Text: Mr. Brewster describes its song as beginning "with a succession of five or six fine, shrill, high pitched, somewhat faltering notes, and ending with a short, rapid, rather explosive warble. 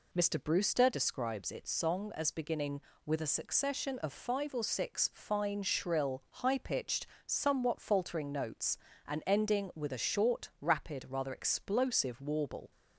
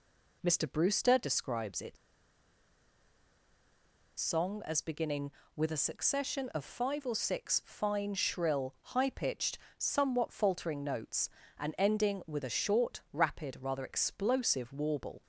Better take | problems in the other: first | pauses between "its" and "song"; strong; at 1.9 s; 2.2 s long

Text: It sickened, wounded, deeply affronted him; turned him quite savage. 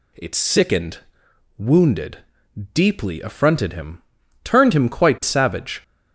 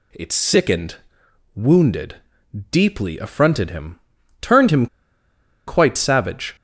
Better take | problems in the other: first | pauses between "him" and "quite"; noticeable; at 4.8 s; 0.80 s long

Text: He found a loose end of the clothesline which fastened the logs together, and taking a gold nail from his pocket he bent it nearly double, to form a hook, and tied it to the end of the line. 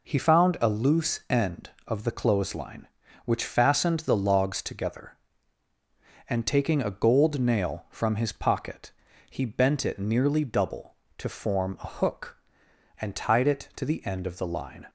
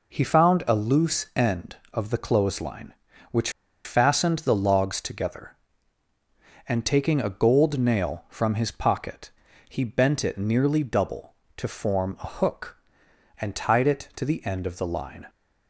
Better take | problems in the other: first | pauses between "which" and "fastened"; slight; at 3.4 s; 0.35 s long // pauses between "pocket" and "he"; at 9.3 s; 0.40 s long; also in the first

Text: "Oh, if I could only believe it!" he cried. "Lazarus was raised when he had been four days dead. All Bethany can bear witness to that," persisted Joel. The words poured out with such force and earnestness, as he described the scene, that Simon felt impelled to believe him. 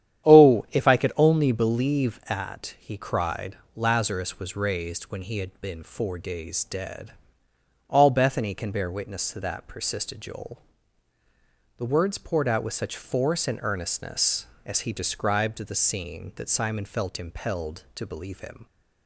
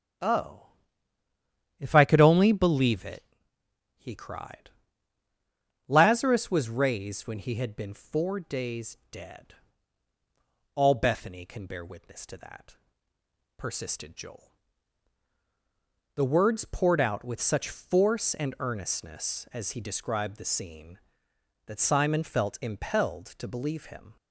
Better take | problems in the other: second | starts louder than the rest; strong; until 1.3 s; 10 dB; strong in the second // says "at" for "it"; at 2.2 s

